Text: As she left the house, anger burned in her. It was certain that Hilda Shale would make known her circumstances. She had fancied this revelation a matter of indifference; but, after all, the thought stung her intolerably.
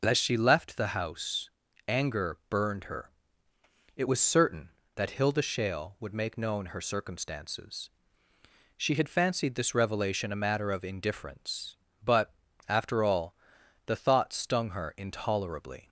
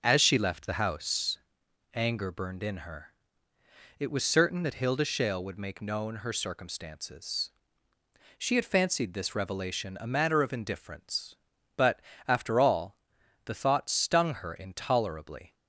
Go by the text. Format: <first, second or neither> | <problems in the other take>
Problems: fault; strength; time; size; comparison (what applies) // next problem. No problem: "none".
second | skips "in"; at 2.8 s